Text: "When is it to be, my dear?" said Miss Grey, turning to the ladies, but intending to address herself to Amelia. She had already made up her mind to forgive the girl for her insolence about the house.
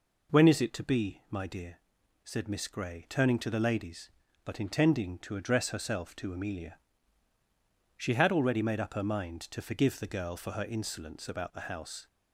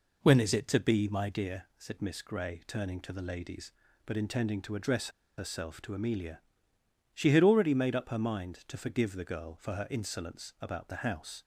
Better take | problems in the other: first | pauses between "address" and "herself"; slight; at 5.0 s; 0.29 s long

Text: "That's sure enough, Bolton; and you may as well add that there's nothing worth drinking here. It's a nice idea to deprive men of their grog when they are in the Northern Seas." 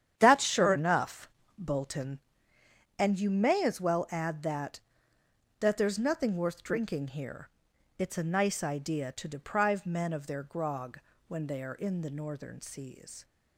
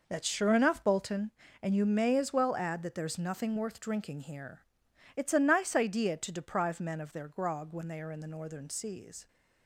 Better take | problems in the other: second | starts louder than the rest; strong; until 1.1 s; 9.5 dB // says "that" twice; at 5.5 s // pauses between "grog" and "when"; slight; at 11.0 s; 0.26 s long

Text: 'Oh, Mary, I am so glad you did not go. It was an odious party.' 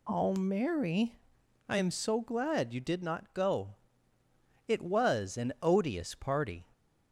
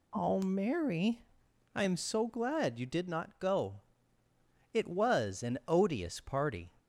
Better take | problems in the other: neither | none

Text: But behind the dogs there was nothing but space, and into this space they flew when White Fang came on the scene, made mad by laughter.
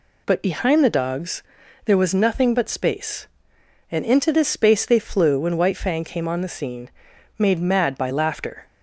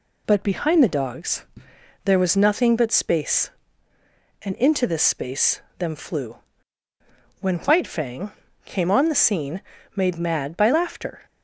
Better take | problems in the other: first | pauses between "dogs" and "there"; noticeable; at 1.4 s; 0.60 s long; also in the first // says "them" for "they"; at 5.7 s // pauses between "flew" and "when"; at 6.3 s; 1.0 s long // pauses between "Fang" and "came"; slight; at 8.3 s; 0.32 s long

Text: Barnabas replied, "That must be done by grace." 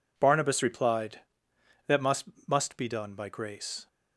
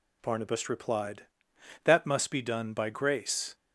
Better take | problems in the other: second | says "must" twice; at 2.4 s

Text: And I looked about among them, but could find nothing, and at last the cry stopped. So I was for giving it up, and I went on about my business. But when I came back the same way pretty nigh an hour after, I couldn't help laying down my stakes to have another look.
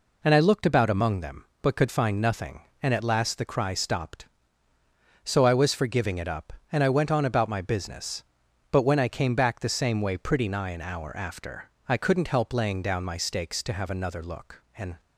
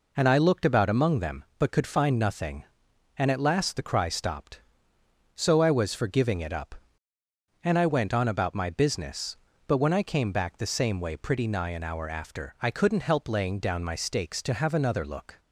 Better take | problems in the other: second | goes on to say "And"; slight; from 14.7 s on; 0.24 s long

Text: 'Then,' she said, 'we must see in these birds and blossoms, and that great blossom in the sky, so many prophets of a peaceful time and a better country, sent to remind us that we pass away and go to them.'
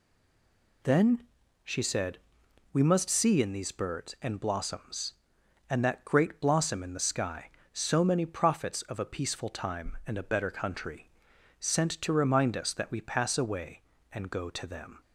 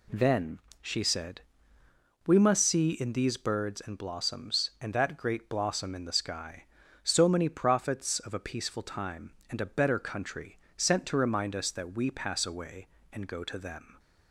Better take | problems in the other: second | stays silent before the first word; slight; until 0.8 s; 0.8 s long

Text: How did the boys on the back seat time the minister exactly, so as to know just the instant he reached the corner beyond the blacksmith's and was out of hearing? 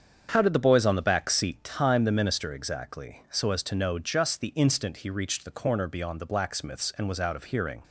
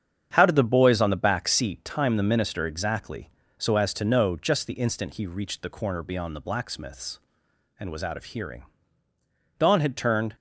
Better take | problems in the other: first | starts louder than the rest; strong; until 1.3 s; 8 dB; strong in the first // goes on to say "Dawn had turned"; noticeable; from 9.5 s on; 0.76 s long

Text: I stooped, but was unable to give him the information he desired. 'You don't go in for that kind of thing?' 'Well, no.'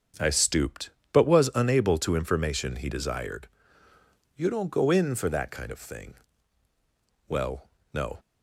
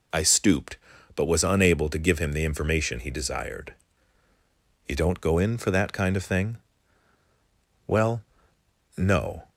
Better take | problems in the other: second | starts louder than the rest; strong; until 1.4 s; 7 dB // skips "give him the"; at 2.1 s

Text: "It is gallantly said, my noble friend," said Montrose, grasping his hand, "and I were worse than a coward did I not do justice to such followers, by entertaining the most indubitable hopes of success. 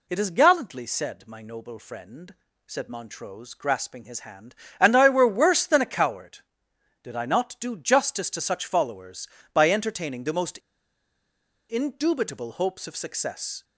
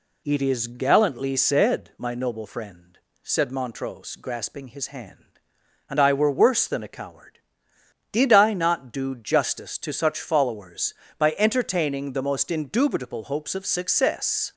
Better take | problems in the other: second | pauses between "most" and "indubitable"; at 10.5 s; 1.1 s long

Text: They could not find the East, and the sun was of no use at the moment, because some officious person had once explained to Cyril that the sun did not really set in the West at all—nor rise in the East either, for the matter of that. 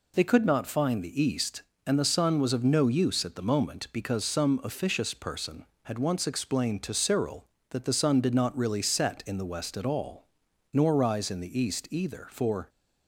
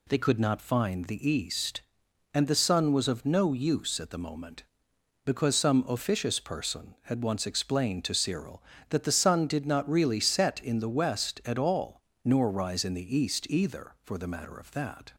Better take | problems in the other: second | stops before "the matter of that"; at 12.6 s

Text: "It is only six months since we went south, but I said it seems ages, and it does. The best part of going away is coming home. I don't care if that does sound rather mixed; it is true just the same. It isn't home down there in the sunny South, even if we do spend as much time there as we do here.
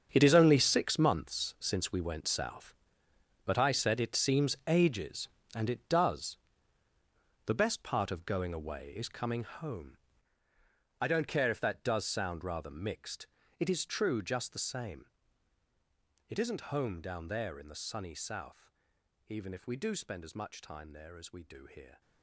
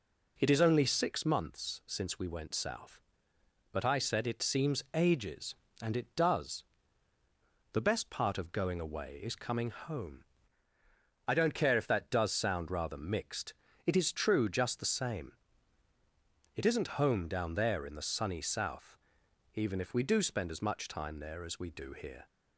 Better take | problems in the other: second | gets quieter; strong; throughout; 13.5 dB

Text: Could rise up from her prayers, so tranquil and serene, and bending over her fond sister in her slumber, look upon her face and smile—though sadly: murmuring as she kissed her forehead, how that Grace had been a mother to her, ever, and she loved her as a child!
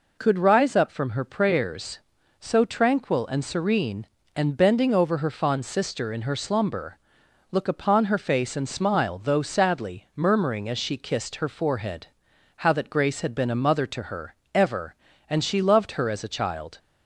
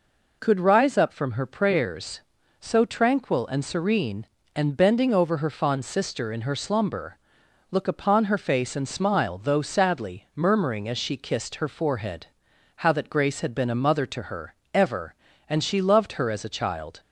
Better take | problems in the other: neither | none

